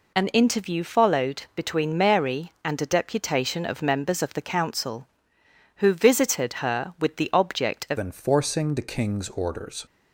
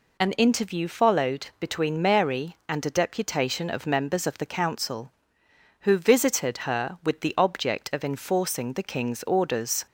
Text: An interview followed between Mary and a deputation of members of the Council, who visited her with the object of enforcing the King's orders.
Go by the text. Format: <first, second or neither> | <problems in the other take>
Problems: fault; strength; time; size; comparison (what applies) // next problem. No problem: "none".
second | changes voice at "enforcing"; from 7.9 s on; 1.9 s long